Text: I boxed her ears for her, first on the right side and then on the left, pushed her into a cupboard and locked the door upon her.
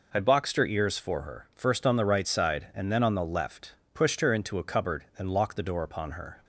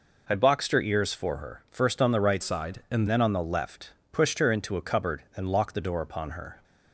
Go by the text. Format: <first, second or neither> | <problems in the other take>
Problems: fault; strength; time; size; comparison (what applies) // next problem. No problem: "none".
first | changes voice from "side" to "and"; from 2.4 to 3.0 s; 0.6 s long